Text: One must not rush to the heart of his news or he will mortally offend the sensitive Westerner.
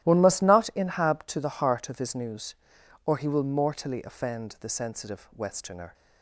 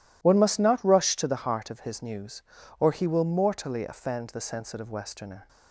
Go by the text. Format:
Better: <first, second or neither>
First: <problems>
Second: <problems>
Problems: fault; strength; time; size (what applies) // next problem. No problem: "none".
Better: second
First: starts louder than the rest; strong; until 1.1 s; 14 dB // says "inhab" for "rush"; at 0.7 s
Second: none